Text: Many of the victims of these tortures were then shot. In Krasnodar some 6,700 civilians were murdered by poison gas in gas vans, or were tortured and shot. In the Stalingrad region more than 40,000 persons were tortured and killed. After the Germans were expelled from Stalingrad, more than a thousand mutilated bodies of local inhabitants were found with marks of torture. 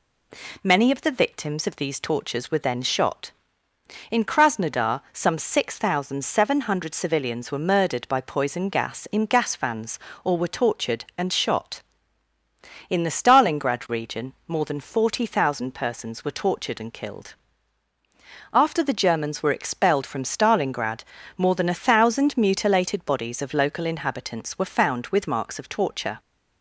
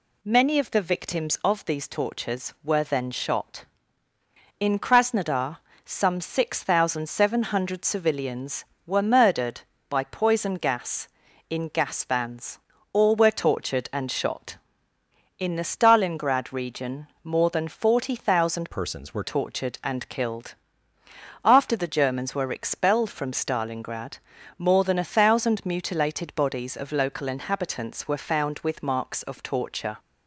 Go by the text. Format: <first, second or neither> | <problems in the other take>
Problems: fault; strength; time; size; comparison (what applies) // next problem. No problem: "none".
first | pauses between "Krasnodar" and "some"; slight; at 5.5 s; 0.26 s long // pauses between "region" and "more"; slight; at 17.0 s; 0.16 s long // changes voice from "persons" to "were"; from 18.7 to 19.2 s; 0.5 s long